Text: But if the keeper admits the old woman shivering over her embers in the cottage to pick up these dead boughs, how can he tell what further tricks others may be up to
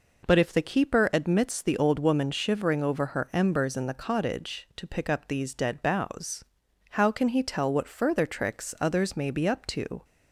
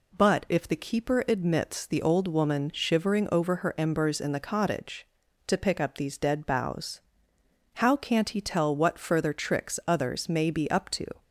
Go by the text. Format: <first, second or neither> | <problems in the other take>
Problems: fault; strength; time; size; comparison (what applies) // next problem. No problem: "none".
first | says "can't" for "can"; at 7.9 s